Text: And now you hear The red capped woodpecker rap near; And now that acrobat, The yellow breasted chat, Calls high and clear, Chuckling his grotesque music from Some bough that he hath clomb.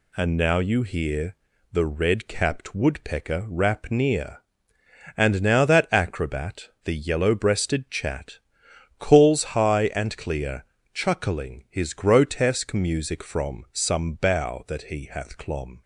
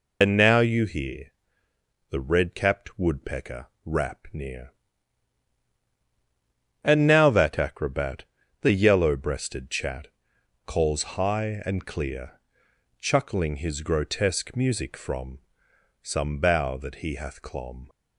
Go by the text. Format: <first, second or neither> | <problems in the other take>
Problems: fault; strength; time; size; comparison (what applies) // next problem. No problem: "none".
first | loses the start of "And"; at 0.2 s; 95 ms // pauses between "hear" and "The"; noticeable; at 1.3 s; 0.80 s long; also in the first // pauses between "woodpecker" and "rap"; slight; at 3.6 s; 0.18 s long // pauses between "from" and "Some"; noticeable; at 15.3 s; 0.64 s long